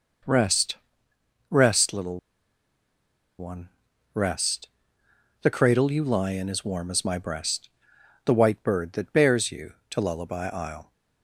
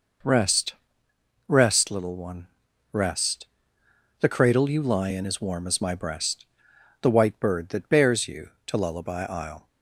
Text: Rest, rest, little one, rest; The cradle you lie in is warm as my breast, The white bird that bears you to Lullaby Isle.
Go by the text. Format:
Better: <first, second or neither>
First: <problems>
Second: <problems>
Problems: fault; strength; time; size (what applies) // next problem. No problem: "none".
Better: second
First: pauses between "little" and "one"; at 2.1 s; 1.2 s long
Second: none